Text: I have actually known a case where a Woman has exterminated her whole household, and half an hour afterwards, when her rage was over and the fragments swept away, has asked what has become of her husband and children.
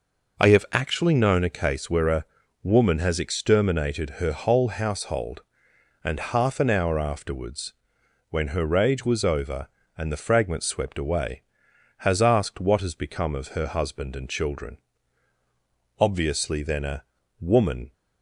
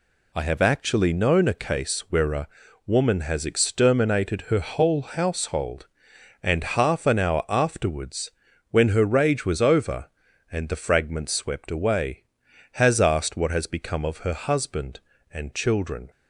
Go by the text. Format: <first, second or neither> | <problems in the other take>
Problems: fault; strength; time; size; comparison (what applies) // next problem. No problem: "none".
second | pauses between "a" and "Woman"; at 2.2 s; 0.38 s long; also in the second // goes on to say "Obviously then a Woman"; strong; from 15.9 s on; 1.9 s long